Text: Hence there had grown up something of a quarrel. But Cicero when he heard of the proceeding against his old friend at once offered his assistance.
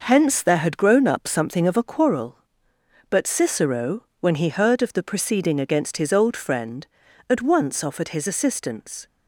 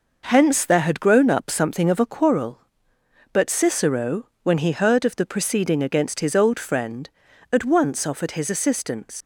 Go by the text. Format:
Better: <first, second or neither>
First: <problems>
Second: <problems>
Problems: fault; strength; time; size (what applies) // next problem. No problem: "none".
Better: first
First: none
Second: leaves "assistance" unfinished; at 9.2 s; 75 ms